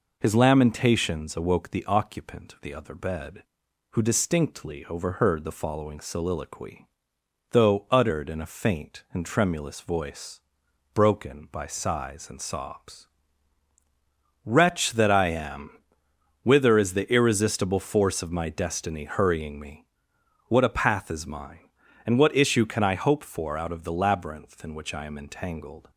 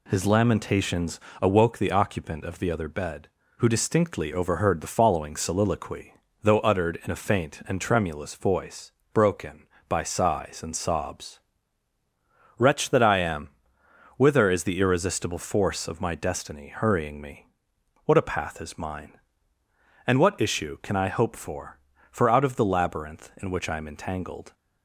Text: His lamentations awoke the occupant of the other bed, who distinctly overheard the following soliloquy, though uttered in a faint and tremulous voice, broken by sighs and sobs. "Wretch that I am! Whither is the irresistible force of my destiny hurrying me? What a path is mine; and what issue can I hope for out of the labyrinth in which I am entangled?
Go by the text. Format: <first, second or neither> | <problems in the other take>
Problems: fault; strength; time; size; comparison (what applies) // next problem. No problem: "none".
first | pauses between "lamentations" and "awoke"; slight; at 1.1 s; 0.22 s long // says "for" twice; at 22.1 s